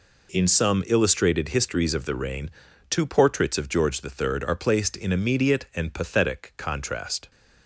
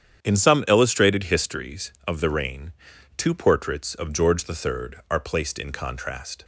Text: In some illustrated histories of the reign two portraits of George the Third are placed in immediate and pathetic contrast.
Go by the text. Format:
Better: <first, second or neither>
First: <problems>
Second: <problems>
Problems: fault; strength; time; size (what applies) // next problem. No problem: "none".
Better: first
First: pauses between "reign" and "two"; at 2.5 s; 0.38 s long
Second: starts louder than the rest; strong; until 1.2 s; 8.5 dB // pauses between "reign" and "two"; at 2.7 s; 0.44 s long // skips "immediate and pathetic"; at 5.7 s